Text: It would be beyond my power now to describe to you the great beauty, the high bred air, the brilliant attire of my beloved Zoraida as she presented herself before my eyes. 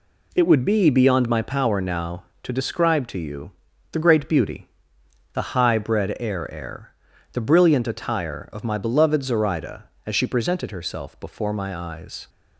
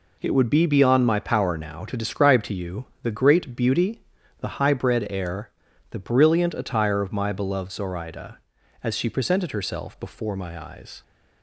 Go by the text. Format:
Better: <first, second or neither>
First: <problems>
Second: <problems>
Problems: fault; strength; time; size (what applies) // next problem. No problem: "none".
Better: second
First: pauses between "you" and "the"; at 3.5 s; 0.40 s long // says "air" twice; at 6.5 s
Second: pauses between "you" and "the"; slight; at 2.8 s; 0.16 s long